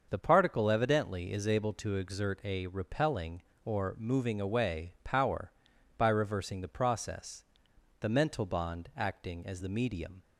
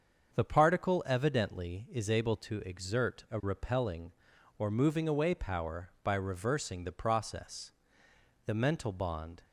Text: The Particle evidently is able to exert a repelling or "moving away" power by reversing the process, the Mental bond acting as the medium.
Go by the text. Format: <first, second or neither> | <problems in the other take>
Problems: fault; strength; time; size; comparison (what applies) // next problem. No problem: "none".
first | starts louder than the rest; until 1.3 s; 7 dB; also in the first // stops before "acting as the medium"; at 9.4 s